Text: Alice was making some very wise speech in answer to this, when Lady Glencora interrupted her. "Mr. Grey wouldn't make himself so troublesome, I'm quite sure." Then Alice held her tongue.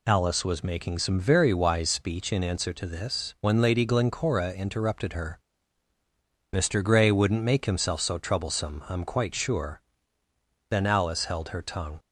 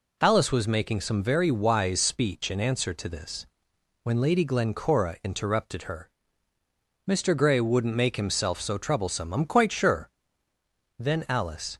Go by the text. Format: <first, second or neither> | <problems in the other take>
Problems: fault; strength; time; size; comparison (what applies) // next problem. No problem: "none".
first | stops before "held her tongue"; at 11.7 s